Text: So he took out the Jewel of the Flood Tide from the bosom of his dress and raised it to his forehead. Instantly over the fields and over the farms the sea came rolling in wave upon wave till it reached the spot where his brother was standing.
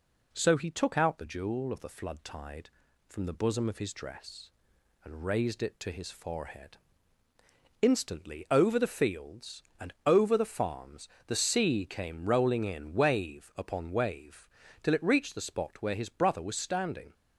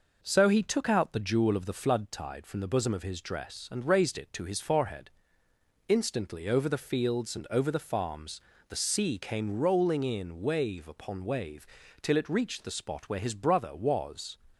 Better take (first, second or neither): first